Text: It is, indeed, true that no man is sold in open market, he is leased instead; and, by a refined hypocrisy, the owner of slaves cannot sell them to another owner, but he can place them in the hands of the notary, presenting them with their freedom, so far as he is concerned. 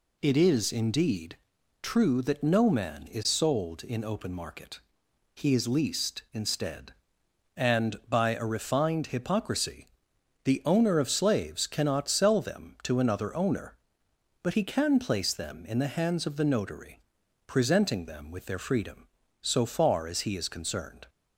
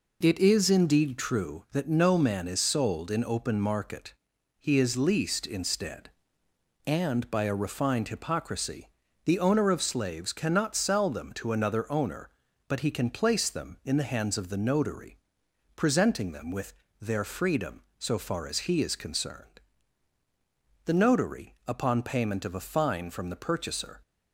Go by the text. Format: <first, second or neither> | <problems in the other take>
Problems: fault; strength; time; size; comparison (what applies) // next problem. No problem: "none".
first | pauses between "with" and "their"; slight; at 16.7 s; 0.26 s long // goes on to say "The notary upon payment of a fine from the purchaser"; strong; from 20.8 s on; 3.1 s long